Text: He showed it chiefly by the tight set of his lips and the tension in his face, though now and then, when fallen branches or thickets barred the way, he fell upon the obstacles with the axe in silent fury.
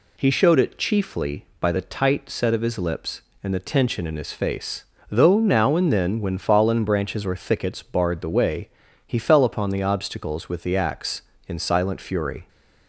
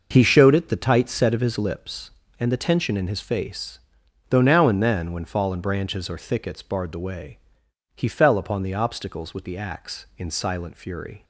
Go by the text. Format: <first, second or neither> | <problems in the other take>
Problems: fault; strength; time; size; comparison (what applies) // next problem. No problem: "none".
first | skips "chiefly by"; at 0.6 s